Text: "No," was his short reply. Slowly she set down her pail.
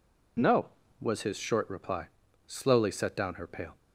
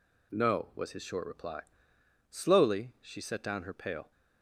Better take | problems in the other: second | skips "she"; at 2.9 s

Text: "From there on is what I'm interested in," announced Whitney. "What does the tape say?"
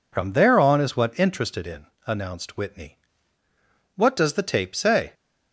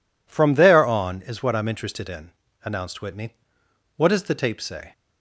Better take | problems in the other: second | skips "I'm"; at 1.1 s

